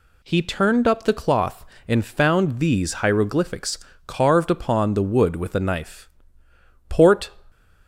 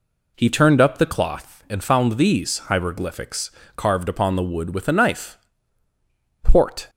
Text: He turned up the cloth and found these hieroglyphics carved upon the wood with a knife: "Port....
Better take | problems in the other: first | starts louder than the rest; slight; until 1.8 s; 3.5 dB // pauses between "hieroglyphics" and "carved"; slight; at 3.5 s; 0.26 s long; slight in the first

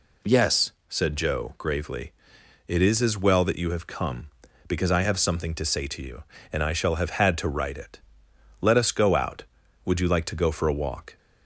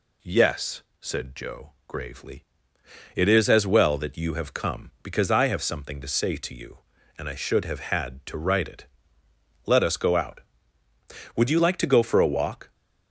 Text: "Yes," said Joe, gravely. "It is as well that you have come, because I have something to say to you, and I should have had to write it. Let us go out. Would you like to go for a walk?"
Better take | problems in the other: second | says "shall" for "should"; at 6.7 s

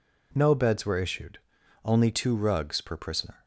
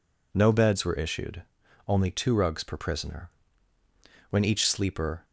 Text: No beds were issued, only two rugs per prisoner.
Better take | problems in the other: first | goes on to say "When each sleeper"; noticeable; from 4.2 s on; 0.96 s long

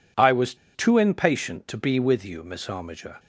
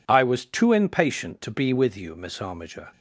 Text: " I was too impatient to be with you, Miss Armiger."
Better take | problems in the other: second | pauses between "was" and "too"; slight; at 0.5 s; 0.19 s long

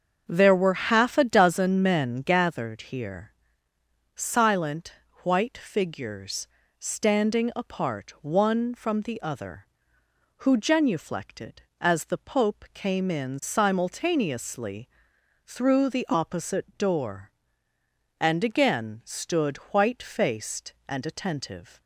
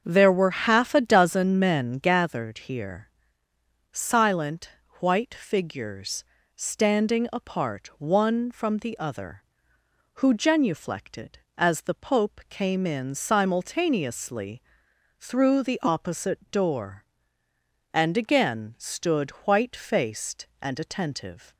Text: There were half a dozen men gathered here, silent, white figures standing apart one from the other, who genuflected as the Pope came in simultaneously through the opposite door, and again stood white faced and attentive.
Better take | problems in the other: neither | starts louder than the rest; the same in both // pauses between "figures" and "standing"; slight; the same in both // pauses between "simultaneously" and "through"; noticeable; the same in both // pauses between "stood" and "white"; slight; the same in both

